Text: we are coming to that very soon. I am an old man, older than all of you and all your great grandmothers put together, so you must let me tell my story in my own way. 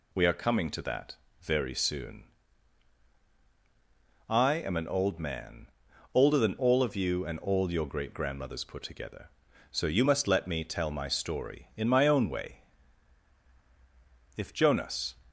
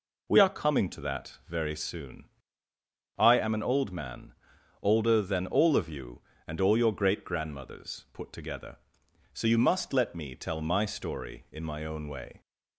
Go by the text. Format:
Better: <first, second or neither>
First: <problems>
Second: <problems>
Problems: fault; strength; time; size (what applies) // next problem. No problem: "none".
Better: second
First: pauses between "that" and "very"; slight; at 1.1 s; 0.26 s long // goes on to say "If Jonas"; noticeable; from 14.3 s on; 0.82 s long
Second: none